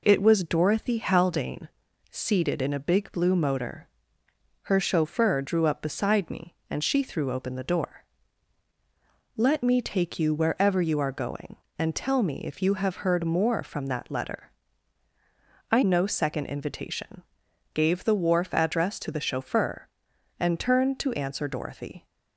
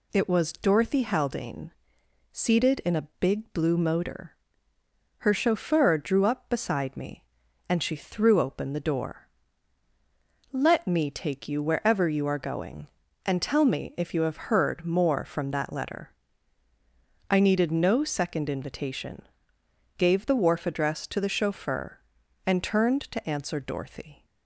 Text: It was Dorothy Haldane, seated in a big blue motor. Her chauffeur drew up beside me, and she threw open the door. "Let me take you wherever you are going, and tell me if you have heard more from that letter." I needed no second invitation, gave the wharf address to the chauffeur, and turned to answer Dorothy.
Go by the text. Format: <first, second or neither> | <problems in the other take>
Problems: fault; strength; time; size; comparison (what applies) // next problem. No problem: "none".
second | skips "needed"; at 15.8 s